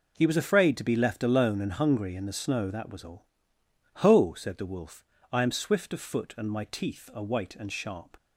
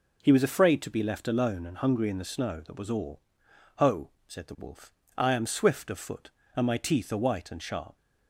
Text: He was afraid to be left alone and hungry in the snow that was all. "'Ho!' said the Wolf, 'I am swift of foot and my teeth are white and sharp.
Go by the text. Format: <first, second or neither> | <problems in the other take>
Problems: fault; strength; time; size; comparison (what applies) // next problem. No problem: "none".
neither | none